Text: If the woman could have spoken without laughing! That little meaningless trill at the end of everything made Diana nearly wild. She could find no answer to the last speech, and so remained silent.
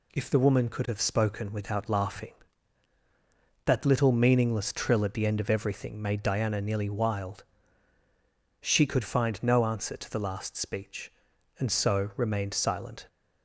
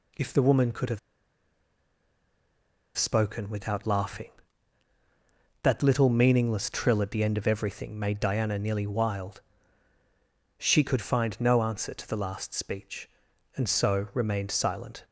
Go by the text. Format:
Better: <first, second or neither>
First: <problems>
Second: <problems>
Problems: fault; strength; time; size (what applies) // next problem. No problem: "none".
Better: first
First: none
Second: pauses between "have" and "spoken"; strong; at 0.9 s; 1.9 s long